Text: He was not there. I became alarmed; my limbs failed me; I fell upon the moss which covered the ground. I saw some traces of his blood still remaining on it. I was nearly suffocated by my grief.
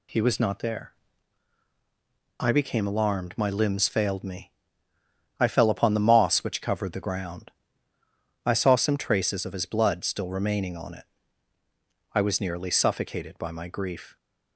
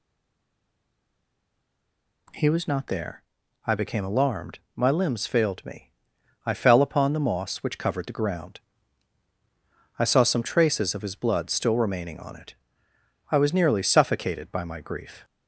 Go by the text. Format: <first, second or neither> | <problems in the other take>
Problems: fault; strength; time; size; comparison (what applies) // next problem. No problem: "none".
first | stays silent before the first word; until 2.2 s; 2.2 s long